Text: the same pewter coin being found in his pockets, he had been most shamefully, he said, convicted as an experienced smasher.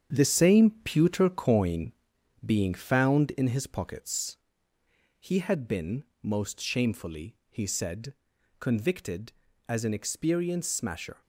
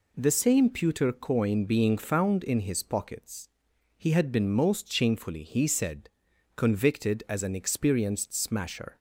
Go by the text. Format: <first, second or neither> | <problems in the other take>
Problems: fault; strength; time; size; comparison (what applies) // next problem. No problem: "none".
second | gets quieter; strong; throughout; 9 dB // pauses between "coin" and "being"; noticeable; at 1.9 s; 0.52 s long // pauses between "been" and "most"; slight; at 6.0 s; 0.18 s long